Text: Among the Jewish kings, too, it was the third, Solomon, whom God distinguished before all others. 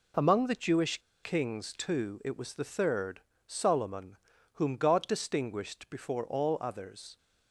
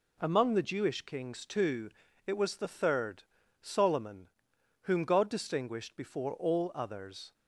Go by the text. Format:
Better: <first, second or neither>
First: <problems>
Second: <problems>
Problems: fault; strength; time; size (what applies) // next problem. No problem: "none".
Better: second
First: pauses between "Jewish" and "kings"; slight; at 0.9 s; 0.25 s long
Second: none